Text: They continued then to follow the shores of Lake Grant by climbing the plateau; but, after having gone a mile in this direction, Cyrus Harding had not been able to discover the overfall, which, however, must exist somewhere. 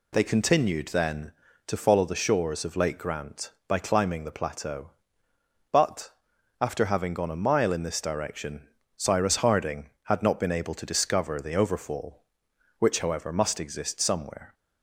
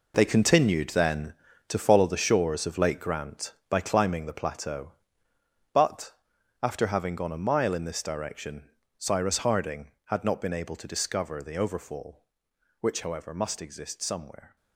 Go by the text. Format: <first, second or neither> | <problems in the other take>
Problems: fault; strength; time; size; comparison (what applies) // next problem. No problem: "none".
first | gets quieter; strong; throughout; 12 dB